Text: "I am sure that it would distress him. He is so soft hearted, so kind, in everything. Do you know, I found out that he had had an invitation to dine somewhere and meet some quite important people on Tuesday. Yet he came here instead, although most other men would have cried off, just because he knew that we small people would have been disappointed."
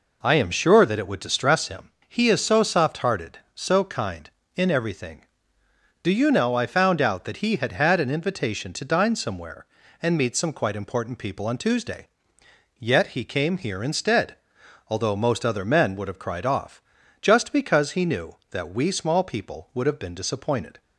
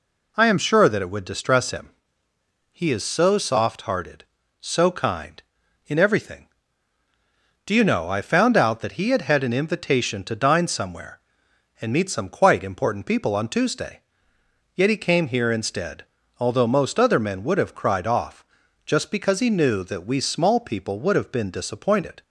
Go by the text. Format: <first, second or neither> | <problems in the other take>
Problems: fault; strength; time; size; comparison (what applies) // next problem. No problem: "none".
neither | none